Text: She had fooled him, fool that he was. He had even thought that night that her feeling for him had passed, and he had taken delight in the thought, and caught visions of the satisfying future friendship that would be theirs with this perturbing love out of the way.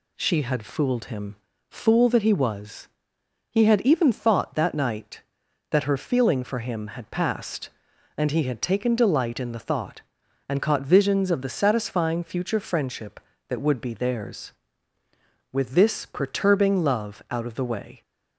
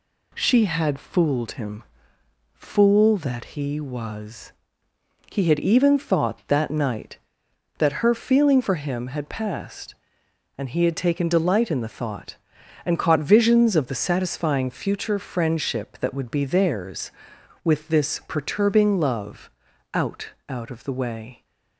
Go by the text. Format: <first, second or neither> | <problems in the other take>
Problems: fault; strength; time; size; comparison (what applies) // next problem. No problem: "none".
first | pauses between "love" and "out"; at 19.5 s; 0.44 s long // says "out" twice; at 20.4 s